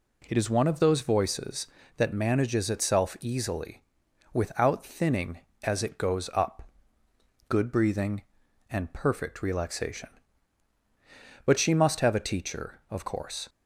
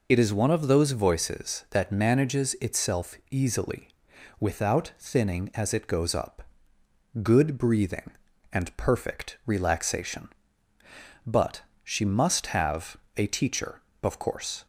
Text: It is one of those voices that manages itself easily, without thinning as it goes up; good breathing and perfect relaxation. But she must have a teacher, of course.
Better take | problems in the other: first | loses the start of "It"; at 0.0 s; 55 ms // pauses between "itself" and "easily"; slight; at 3.1 s; 0.16 s long // pauses between "But" and "she"; slight; at 11.6 s; 0.24 s long // pauses between "have" and "a"; slight; at 12.9 s; 0.18 s long

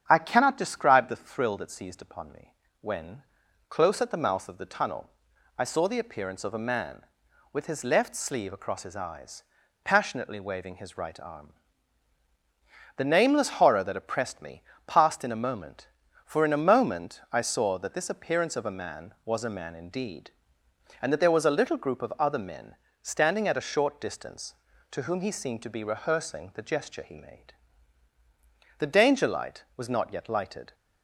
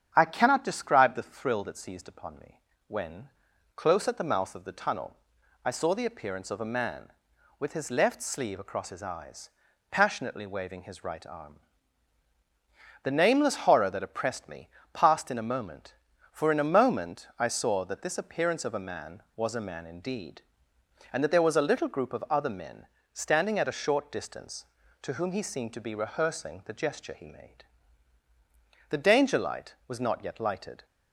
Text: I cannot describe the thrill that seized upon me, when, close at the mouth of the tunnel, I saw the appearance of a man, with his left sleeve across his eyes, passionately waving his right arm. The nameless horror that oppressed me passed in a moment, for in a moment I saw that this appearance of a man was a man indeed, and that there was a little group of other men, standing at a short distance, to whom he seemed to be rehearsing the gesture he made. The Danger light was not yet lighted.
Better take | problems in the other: neither | starts louder than the rest; strong; the same in both // pauses between "me" and "passed"; slight; the same in both

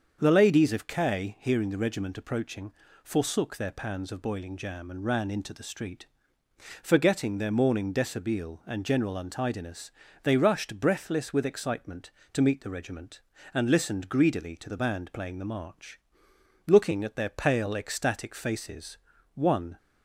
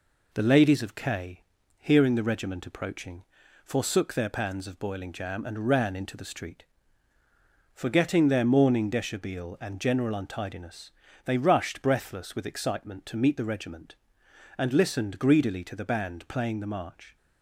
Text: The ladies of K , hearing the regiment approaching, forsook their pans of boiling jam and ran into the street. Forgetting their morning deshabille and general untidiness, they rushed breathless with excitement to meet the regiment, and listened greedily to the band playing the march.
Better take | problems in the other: second | starts louder than the rest; until 1.2 s; 7 dB // goes on to say "Looking at their pale ecstatic faces one"; strong; from 16.6 s on; 3.1 s long

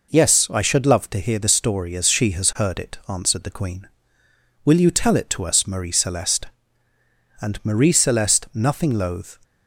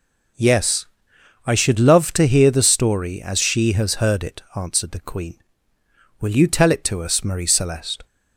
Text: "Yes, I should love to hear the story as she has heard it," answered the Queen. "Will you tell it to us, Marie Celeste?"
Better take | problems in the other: second | goes on to say "And Marie Celeste nothing loath"; strong; from 7.4 s on; 2.0 s long

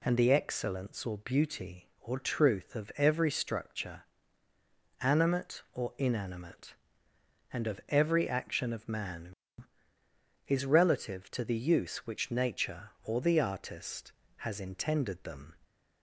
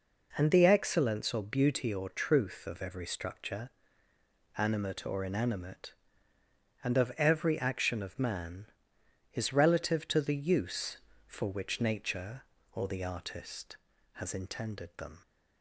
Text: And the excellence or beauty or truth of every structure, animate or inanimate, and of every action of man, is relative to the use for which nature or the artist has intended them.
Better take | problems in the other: second | skips "for"; at 11.9 s

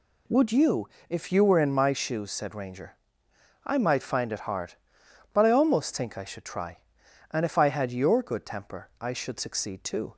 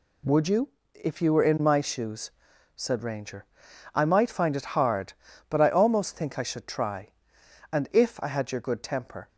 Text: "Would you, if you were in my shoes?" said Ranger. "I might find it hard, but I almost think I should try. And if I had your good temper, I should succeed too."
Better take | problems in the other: first | stops before "I should succeed too"; at 9.2 s

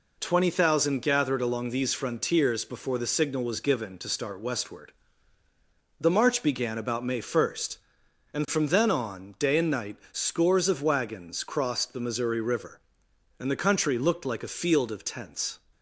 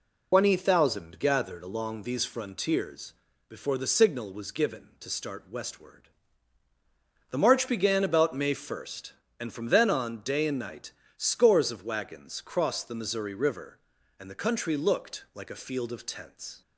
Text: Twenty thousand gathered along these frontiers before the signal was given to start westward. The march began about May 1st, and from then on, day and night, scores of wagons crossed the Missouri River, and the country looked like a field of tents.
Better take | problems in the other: first | loses the start of "Twenty"; at 0.3 s; 140 ms // pauses between "frontiers" and "before"; slight; at 3.1 s; 0.36 s long

